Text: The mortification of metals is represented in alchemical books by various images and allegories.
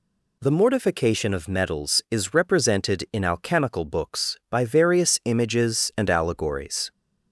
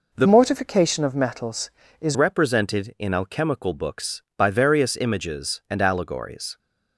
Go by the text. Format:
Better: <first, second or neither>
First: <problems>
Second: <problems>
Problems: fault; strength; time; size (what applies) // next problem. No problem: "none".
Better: first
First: none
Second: changes voice from "mortification" to "is"; from 0.2 to 2.1 s; 1.9 s long